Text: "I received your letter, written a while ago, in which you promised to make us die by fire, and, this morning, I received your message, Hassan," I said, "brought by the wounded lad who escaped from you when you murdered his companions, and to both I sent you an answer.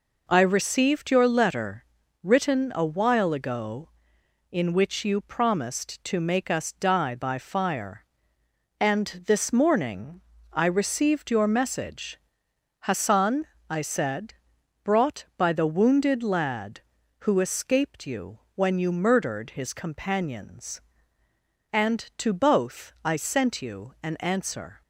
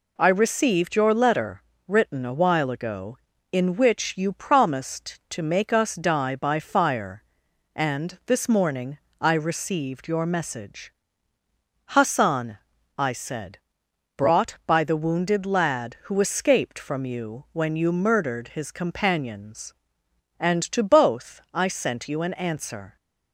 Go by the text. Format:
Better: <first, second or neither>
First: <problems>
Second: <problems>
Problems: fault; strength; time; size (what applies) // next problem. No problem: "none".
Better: second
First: skips "from"; at 18.0 s // pauses between "you" and "when"; slight; at 18.3 s; 0.18 s long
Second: none